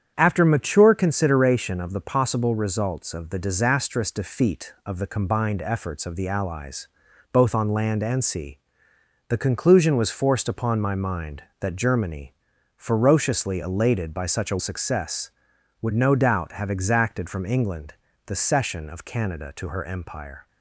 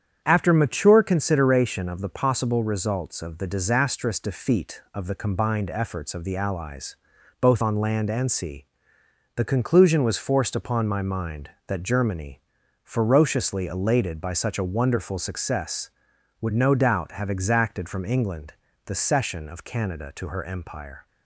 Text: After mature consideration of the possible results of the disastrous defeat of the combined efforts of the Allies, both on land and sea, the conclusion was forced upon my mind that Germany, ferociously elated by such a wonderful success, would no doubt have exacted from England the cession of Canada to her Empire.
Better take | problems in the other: second | starts louder than the rest; strong; until 1.1 s; 8.5 dB; strong in the second // skips "wonderful"; at 14.5 s // pauses between "England" and "the"; slight; at 17.9 s; 0.32 s long; slight in the second

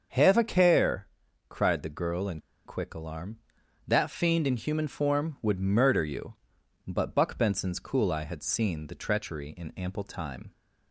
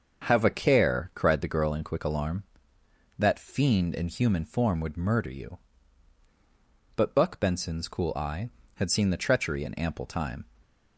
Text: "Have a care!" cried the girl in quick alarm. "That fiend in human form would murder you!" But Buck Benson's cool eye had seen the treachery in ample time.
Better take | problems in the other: second | starts louder than the rest; until 1.5 s; 6.5 dB; also in the second // pauses between "in" and "quick"; slight; at 2.3 s; 0.26 s long

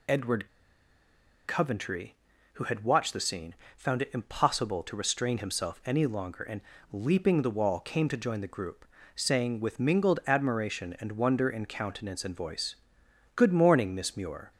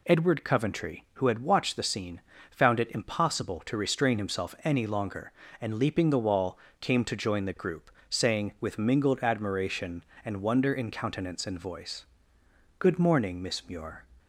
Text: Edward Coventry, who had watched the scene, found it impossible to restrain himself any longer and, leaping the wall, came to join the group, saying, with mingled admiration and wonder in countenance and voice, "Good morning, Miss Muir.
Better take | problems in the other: second | pauses between "Edward" and "Coventry"; at 0.4 s; 0.98 s long

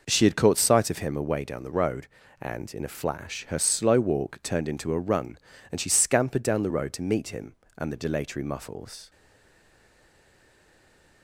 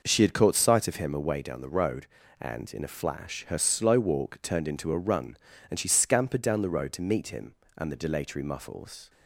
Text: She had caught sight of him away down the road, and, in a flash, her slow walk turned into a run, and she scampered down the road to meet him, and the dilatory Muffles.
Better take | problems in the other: second | stays silent after the last word; from 9.0 s on; 2.2 s long

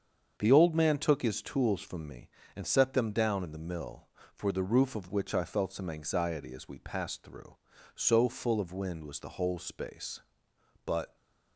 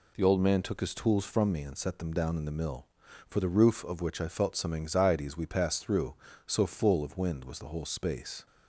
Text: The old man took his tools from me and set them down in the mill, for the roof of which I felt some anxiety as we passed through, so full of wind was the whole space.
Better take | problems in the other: second | starts louder than the rest; strong; until 1.4 s; 7 dB // goes on to say "But"; slight; from 10.8 s on; 0.32 s long

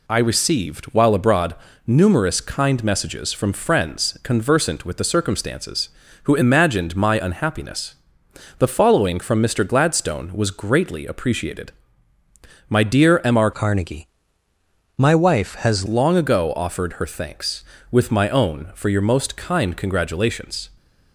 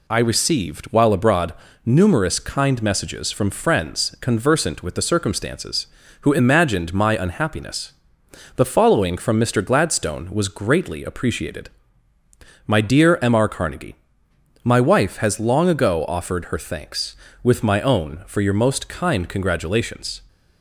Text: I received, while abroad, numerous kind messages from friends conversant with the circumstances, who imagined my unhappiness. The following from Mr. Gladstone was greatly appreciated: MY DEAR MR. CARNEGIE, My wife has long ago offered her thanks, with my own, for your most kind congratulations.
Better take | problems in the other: second | changes voice from "CARNEGIE" to "has"; from 13.5 to 15.8 s; 2.3 s long

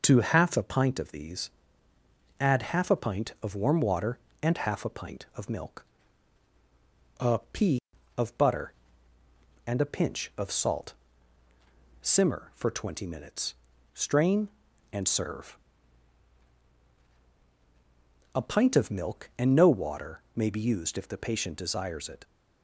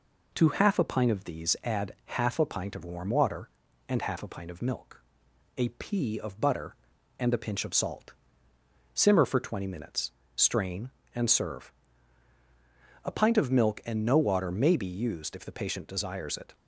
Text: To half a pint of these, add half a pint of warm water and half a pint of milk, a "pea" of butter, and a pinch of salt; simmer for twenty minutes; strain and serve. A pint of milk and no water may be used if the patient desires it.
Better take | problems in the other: neither | none

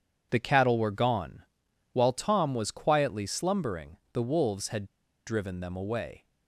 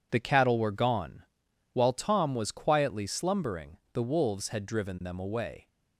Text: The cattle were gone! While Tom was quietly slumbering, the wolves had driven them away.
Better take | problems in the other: second | pauses between "had" and "driven"; at 4.8 s; 0.41 s long

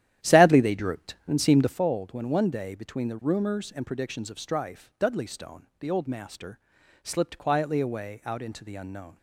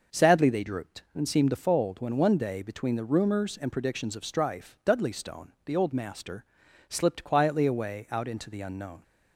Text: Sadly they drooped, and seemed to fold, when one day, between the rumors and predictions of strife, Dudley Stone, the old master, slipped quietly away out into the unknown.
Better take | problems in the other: second | starts louder than the rest; strong; until 1.8 s; 11.5 dB

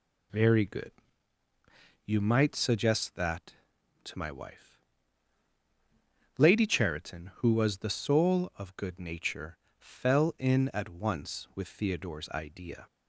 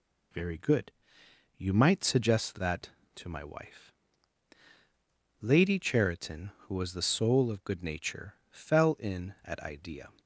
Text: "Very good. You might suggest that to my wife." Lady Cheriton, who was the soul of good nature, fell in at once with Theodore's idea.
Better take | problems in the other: first | skips "once with Theodore's"; at 9.5 s

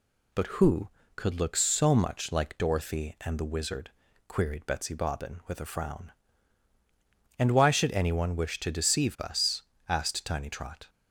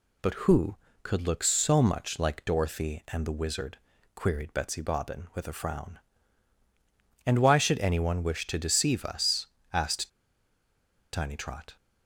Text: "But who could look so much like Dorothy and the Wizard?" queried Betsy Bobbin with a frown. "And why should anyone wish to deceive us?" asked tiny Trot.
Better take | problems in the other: first | pauses between "asked" and "tiny"; at 10.0 s; 1.0 s long

